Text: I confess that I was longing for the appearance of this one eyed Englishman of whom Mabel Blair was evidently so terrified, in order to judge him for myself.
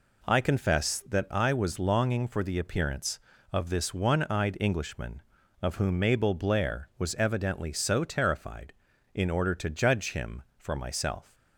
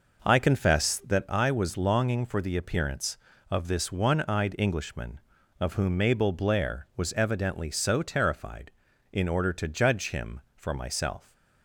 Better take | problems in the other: first | starts louder than the rest; noticeable; until 1.2 s; 5.5 dB

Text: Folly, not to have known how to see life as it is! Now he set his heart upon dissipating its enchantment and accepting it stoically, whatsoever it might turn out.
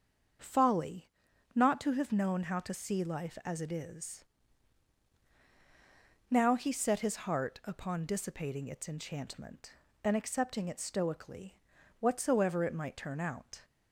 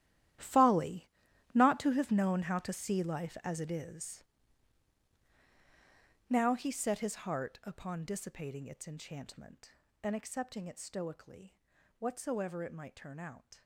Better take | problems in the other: first | gets quieter; strong; throughout; 16.5 dB // starts louder than the rest; strong; until 1.8 s; 12 dB; also in the first

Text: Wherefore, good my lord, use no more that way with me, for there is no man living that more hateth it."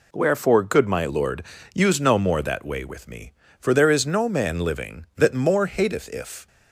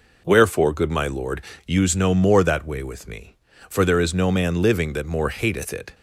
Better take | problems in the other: second | says "if" for "it"; at 6.0 s

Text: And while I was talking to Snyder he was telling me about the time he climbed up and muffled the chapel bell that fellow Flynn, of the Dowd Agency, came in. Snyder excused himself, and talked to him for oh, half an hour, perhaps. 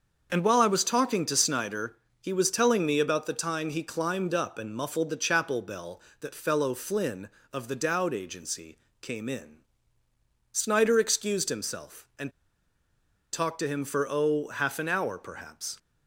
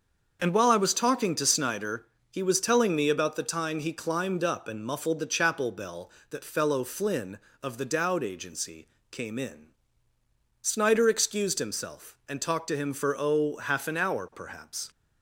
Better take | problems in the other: second | starts louder than the rest; until 1.3 s; 6.5 dB; also in the second // pauses between "Snyder" and "he"; slight; at 1.9 s; 0.26 s long; slight in the second // pauses between "and" and "talked"; at 12.3 s; 1.0 s long

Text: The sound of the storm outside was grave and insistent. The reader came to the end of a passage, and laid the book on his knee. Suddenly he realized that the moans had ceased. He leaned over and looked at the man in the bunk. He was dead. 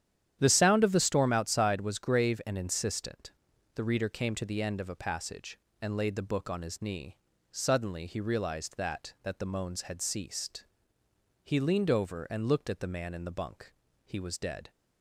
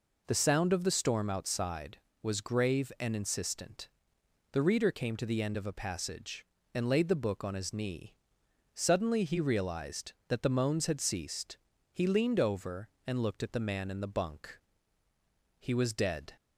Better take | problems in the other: second | starts louder than the rest; strong; until 1.4 s; 10 dB // says "that" twice; at 9.2 s

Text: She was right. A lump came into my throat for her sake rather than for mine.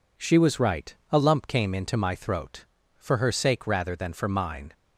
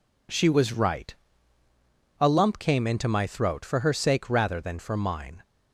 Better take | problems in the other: neither | none

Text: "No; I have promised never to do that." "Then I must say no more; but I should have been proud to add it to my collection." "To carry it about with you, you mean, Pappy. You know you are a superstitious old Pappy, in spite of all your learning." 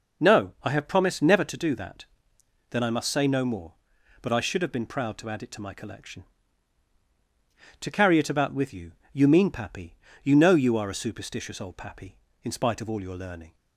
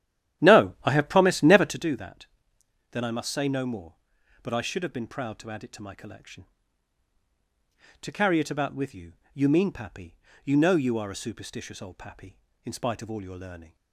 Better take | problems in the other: first | starts louder than the rest; strong; until 2.0 s; 11.5 dB

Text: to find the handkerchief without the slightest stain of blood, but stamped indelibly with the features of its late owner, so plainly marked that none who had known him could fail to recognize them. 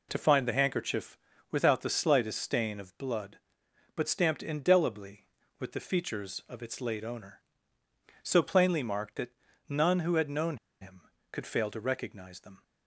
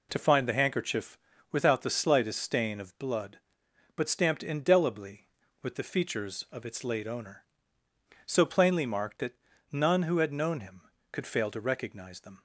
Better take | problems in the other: second | pauses between "handkerchief" and "without"; slight; at 1.1 s; 0.36 s long; slight in the second // pauses between "that" and "none"; slight; at 9.3 s; 0.36 s long; slight in the second // pauses between "known" and "him"; slight; at 10.5 s; 0.23 s long

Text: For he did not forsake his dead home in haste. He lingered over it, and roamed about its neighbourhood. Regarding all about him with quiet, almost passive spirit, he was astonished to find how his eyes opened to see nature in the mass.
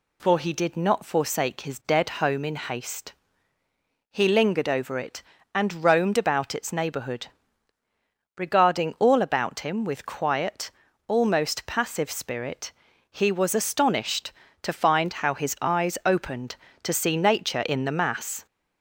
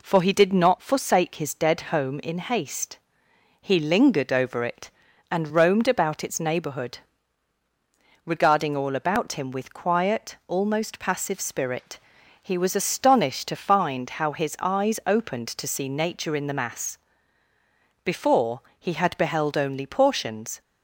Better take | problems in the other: first | goes on to say "Before he had beheld only portions"; strong; from 18.0 s on; 2.5 s long

